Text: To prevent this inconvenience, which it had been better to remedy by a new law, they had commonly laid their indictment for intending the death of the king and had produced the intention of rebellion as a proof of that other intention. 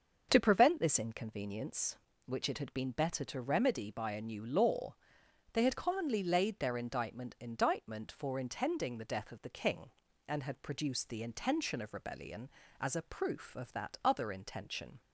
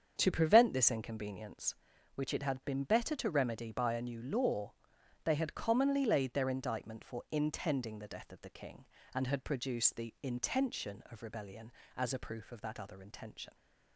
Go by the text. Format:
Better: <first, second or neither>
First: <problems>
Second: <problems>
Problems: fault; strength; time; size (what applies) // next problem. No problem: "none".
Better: second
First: starts louder than the rest; until 1.3 s; 6.5 dB // says "indictment" twice; at 7.3 s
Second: starts louder than the rest; strong; until 1.1 s; 7.5 dB